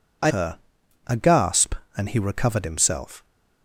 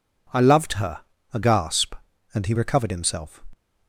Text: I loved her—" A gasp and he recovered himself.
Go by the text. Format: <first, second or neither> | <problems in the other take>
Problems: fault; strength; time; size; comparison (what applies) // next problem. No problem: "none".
second | skips "loved"; at 0.3 s